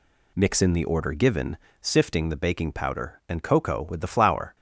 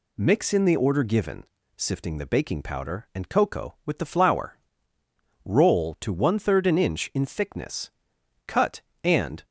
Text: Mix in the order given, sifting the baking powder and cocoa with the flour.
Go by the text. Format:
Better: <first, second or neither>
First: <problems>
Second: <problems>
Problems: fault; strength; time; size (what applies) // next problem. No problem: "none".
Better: first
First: none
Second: goes on to say "Roll to one third an inch in thickness cut and"; strong; from 5.4 s on; 4.0 s long